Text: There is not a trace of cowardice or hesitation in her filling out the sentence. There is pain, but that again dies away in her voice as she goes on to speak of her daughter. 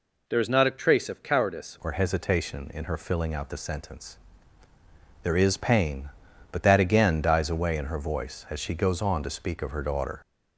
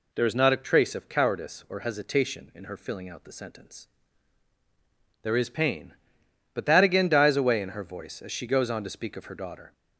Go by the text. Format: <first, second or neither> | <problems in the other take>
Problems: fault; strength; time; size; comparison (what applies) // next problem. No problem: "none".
second | changes voice at "or"; from 1.8 s on; 8.4 s long